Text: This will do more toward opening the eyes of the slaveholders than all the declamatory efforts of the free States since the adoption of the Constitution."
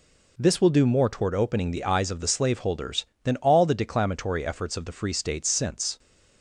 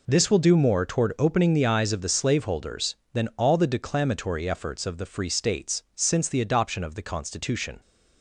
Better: second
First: stops before "the adoption of the Constitution"; at 5.9 s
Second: none

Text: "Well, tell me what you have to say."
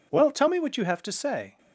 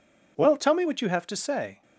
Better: neither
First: none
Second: none

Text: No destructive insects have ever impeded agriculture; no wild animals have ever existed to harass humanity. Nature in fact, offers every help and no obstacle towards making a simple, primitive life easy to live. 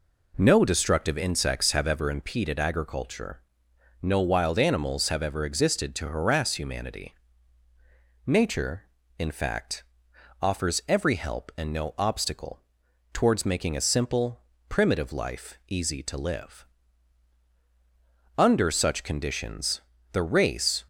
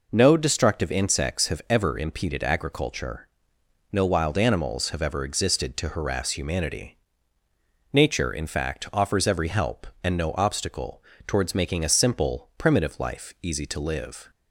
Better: second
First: pauses between "obstacle" and "towards"; noticeable; at 12.6 s; 0.50 s long // goes on to say "Under such conditions the race"; strong; from 18.3 s on; 2.4 s long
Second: pauses between "obstacle" and "towards"; slight; at 11.0 s; 0.24 s long

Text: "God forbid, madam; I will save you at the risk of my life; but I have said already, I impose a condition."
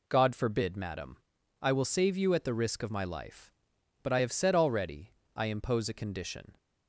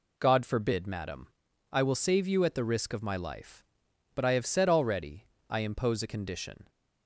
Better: neither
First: none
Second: none

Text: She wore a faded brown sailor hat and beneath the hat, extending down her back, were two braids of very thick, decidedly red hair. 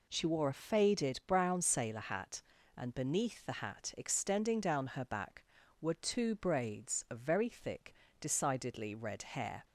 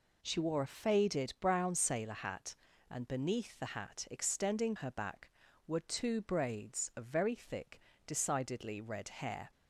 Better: first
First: none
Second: skips "down"; at 4.7 s

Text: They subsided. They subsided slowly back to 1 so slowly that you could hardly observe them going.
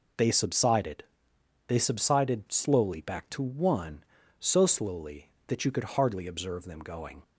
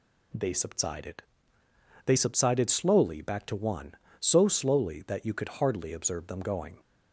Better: neither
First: none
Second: none

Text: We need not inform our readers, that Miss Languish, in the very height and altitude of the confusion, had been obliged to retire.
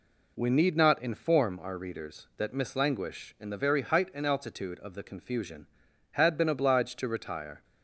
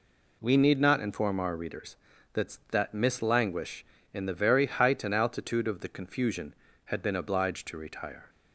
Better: first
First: none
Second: says "that" twice; at 2.7 s

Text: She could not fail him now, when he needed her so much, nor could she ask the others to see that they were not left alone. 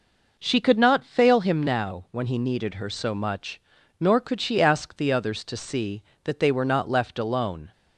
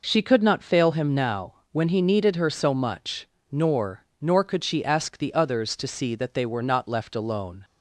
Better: first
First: none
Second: says "nor" twice; at 4.2 s

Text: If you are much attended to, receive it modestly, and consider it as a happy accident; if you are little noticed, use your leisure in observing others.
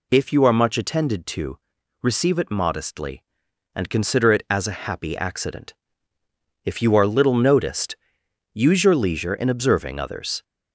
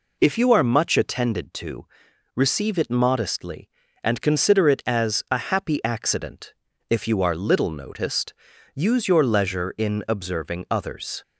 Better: neither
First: none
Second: none

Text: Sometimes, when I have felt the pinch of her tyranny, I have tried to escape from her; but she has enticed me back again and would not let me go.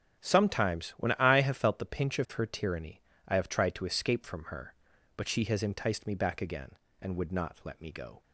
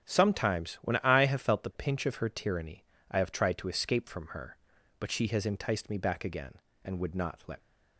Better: first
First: starts louder than the rest; until 1.2 s; 7 dB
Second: starts louder than the rest; until 1.0 s; 6.5 dB // stops before "me go"; at 7.6 s

